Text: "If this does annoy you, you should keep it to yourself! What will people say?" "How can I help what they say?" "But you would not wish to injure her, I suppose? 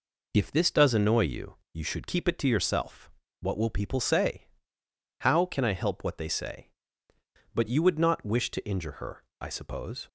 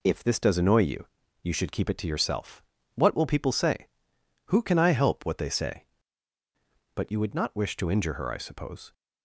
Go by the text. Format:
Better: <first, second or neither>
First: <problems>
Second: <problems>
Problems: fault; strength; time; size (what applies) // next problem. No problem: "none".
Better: first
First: none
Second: says "Who" for "How"; at 4.4 s